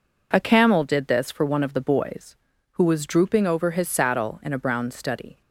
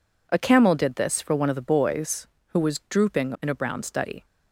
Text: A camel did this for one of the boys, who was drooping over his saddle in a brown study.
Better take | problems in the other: first | skips "over his saddle"; at 3.3 s

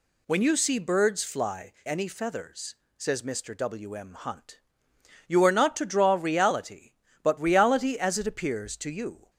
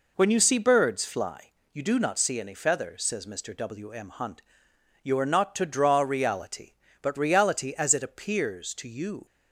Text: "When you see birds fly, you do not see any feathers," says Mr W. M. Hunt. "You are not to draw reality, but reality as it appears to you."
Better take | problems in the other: second | skips "you do not see"; at 1.7 s

